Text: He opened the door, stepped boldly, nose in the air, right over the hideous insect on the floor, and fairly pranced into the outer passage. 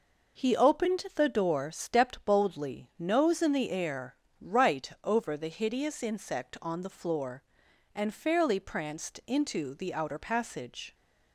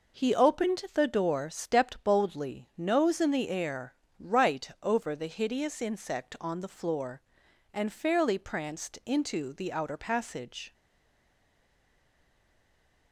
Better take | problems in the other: first | pauses between "right" and "over"; slight; at 4.6 s; 0.16 s long; slight in the first // stays silent after the last word; from 10.7 s on; 2.4 s long

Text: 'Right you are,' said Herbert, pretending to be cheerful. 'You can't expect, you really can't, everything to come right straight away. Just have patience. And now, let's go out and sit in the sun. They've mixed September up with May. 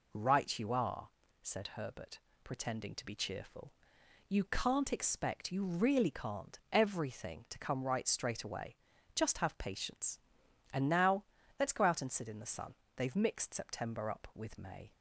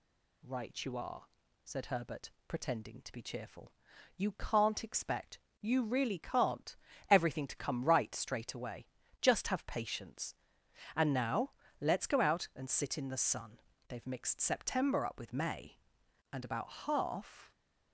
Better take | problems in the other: first | goes on to say "And about half"; noticeable; from 16.3 s on; 1.2 s long

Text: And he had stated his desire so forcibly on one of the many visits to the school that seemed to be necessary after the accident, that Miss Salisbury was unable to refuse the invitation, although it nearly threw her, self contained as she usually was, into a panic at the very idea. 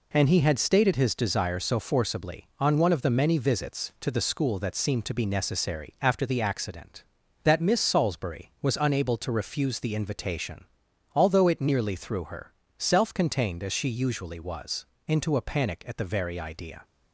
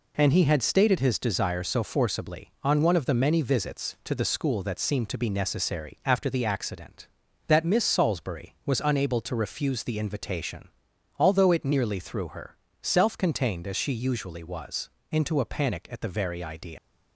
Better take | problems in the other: first | leaves "idea" unfinished; at 16.7 s; 95 ms

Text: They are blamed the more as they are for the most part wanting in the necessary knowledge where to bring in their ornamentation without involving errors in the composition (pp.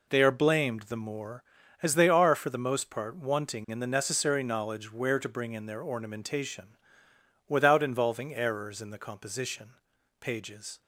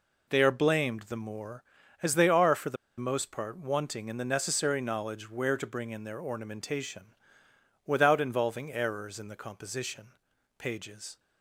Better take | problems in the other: first | pauses between "the" and "most"; slight; at 2.7 s; 0.22 s long // pauses between "ornamentation" and "without"; noticeable; at 7.1 s; 0.74 s long; noticeable in the first

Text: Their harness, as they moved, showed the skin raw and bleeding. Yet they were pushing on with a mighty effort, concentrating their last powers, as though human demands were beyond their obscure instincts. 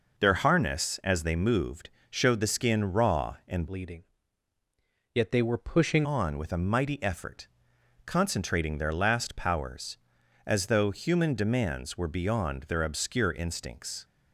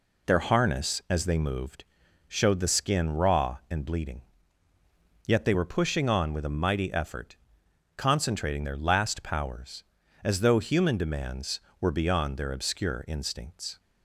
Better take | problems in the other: second | changes voice from "bleeding" to "pushing"; from 3.6 to 6.0 s; 2.4 s long

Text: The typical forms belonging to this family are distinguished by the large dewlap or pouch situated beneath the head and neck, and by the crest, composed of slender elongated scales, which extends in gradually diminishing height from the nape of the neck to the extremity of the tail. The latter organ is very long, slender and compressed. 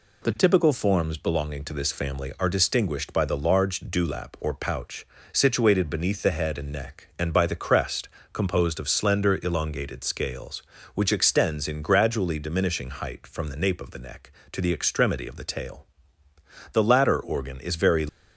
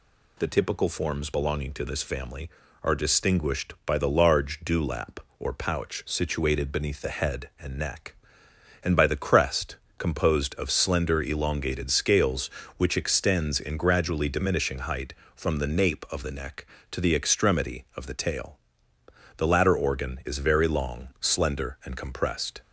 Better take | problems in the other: second | pauses between "pouch" and "situated"; slight; at 5.0 s; 0.26 s long // stops before "long slender and compressed"; at 18.0 s

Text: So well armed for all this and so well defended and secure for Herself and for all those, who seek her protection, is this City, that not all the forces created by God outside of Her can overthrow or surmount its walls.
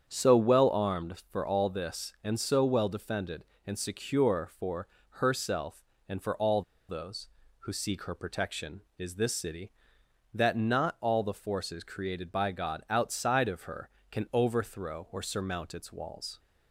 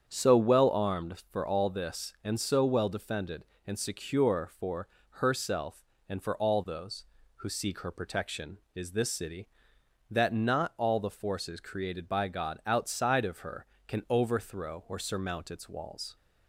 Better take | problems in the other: second | starts louder than the rest; strong; until 1.0 s; 7 dB; strong in the second // pauses between "for" and "Herself"; slight; at 4.8 s; 0.32 s long; slight in the second // pauses between "all" and "those"; slight; at 6.6 s; 0.27 s long

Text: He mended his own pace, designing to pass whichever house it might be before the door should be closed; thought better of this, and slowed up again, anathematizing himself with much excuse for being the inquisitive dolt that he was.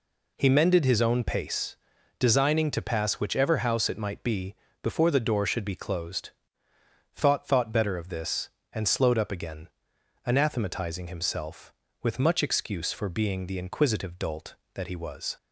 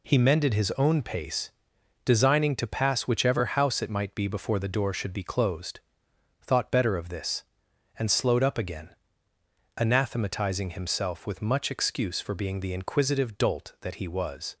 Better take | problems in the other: second | pauses between "be" and "before"; slight; at 4.5 s; 0.28 s long // says "thought" twice; at 7.4 s

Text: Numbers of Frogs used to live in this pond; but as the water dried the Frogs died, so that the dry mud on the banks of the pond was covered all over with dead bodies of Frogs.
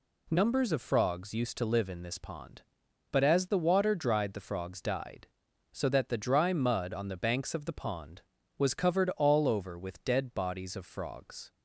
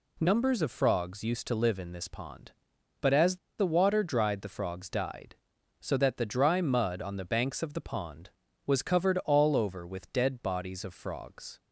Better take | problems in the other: first | pauses between "as" and "the"; slight; at 3.3 s; 0.22 s long

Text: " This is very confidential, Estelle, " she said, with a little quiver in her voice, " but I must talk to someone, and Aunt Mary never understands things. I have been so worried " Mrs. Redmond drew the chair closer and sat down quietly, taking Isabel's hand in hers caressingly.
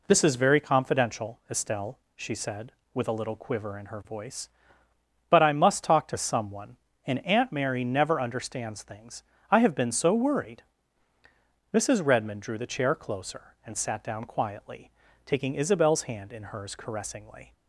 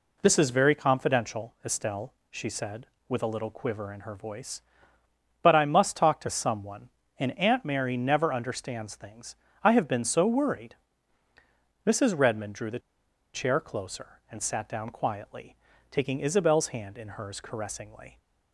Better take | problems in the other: first | pauses between "the" and "chair"; noticeable; at 12.8 s; 0.54 s long

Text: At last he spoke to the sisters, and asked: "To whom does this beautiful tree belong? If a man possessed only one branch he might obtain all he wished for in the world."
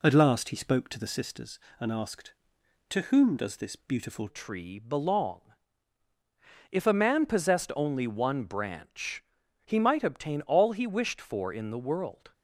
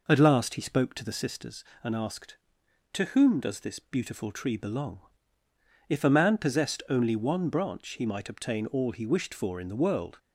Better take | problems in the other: second | changes voice at "tree"; from 4.2 s on; 8.1 s long // pauses between "branch" and "he"; at 9.2 s; 0.44 s long

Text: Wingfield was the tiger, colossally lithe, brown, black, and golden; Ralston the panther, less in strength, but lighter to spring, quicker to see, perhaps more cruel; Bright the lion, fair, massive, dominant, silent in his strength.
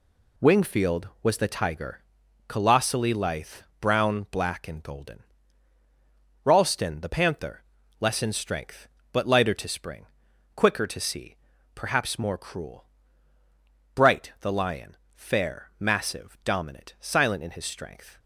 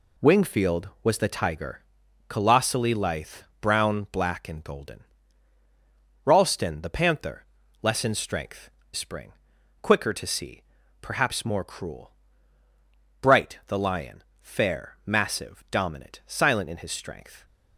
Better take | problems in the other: first | skips "but lighter to"; at 8.8 s

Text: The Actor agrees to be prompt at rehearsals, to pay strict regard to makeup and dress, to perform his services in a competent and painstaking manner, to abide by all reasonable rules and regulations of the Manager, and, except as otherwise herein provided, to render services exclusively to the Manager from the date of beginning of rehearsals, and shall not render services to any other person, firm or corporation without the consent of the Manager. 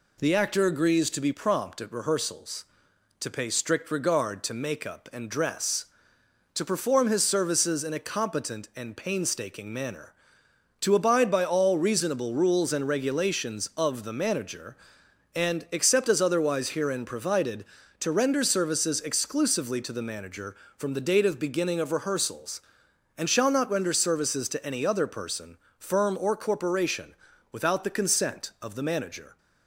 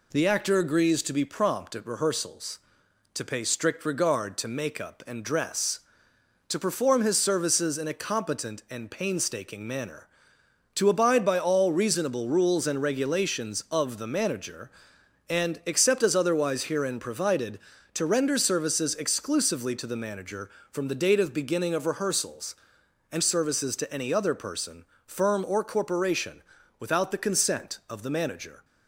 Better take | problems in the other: first | skips "shall not render"; at 23.2 s // pauses between "corporation" and "without"; at 26.4 s; 0.38 s long; also in the first

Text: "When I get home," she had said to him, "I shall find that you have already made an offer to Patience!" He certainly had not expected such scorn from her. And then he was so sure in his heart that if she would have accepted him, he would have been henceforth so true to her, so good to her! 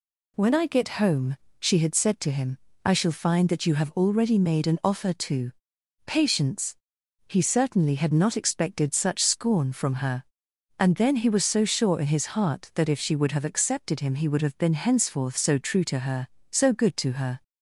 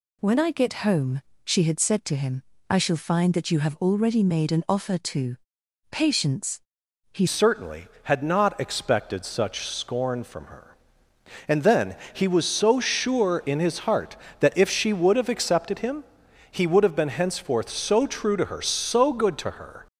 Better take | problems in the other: first | pauses between "to" and "Patience"; noticeable; at 5.3 s; 0.56 s long; noticeable in the first // changes voice at "certainly"; from 7.2 s on; 12.6 s long // pauses between "then" and "he"; slight; at 11.9 s; 0.16 s long

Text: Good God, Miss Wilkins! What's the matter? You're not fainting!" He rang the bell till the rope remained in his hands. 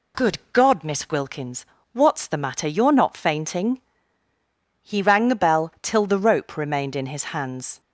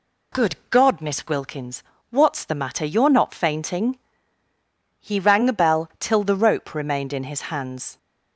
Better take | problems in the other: neither | pauses between "Good" and "God"; slight; the same in both

